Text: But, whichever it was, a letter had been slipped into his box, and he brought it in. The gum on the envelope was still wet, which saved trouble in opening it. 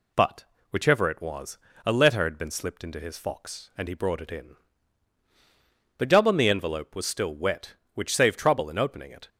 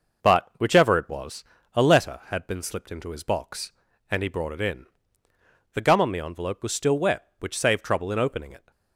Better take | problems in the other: second | says "fox" for "box"; at 3.1 s

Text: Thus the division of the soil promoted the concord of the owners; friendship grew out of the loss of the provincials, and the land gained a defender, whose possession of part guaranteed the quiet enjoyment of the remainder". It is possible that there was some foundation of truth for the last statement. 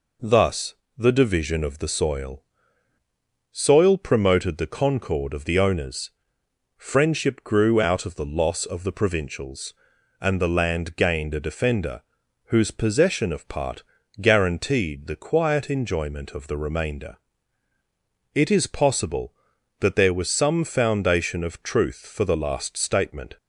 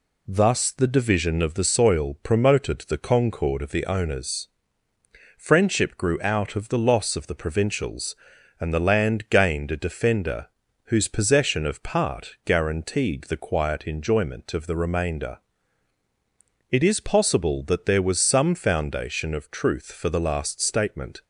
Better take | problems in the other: second | pauses between "Thus" and "the"; slight; at 0.7 s; 0.22 s long // says "soil" twice; at 3.5 s // pauses between "part" and "guaranteed"; at 13.8 s; 0.38 s long

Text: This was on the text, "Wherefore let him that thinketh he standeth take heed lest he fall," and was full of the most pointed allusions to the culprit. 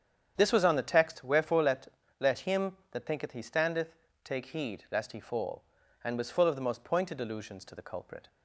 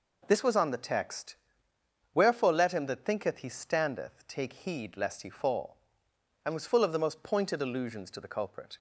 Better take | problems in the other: second | starts louder than the rest; strong; until 1.3 s; 8.5 dB // says "let" twice; at 2.1 s // pauses between "standeth" and "take"; slight; at 3.9 s; 0.30 s long

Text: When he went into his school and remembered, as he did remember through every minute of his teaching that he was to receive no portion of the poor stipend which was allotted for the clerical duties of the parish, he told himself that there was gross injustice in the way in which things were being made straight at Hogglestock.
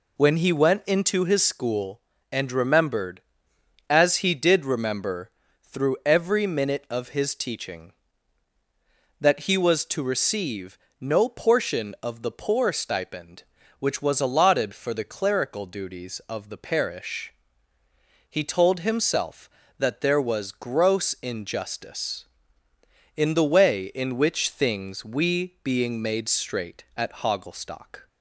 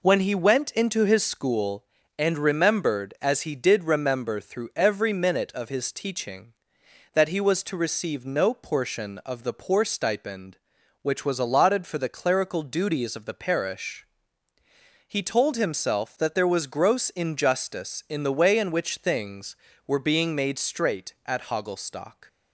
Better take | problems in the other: second | pauses between "remember" and "through"; slight; at 5.2 s; 0.32 s long // pauses between "receive" and "no"; slight; at 10.7 s; 0.24 s long // says "we" for "were"; at 25.0 s

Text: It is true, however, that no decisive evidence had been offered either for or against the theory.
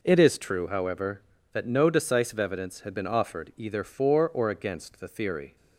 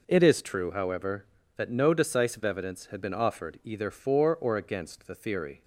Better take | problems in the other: neither | none

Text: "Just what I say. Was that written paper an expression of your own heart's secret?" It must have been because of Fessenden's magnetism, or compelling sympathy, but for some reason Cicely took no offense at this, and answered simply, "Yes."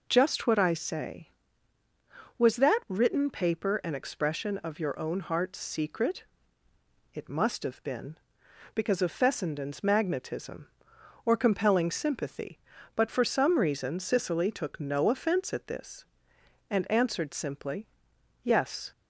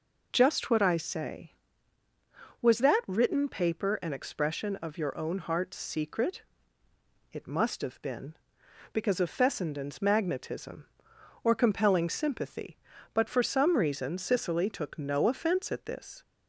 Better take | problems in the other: first | stops before "and answered simply Yes"; at 16.2 s

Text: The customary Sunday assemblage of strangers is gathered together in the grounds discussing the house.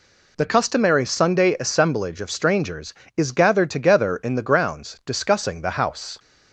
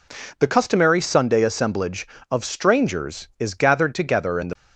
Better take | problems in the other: first | stops before "grounds discussing the house"; at 4.5 s

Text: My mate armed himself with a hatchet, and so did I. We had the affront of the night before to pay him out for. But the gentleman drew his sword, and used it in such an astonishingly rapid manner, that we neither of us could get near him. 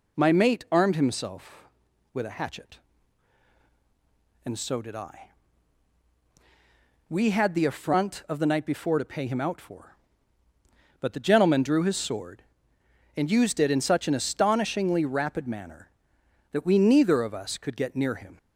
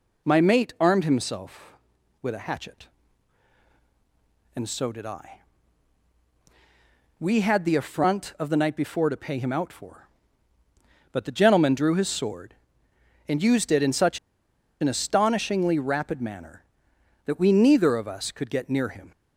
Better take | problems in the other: first | pauses between "such" and "an"; noticeable; at 14.1 s; 0.62 s long

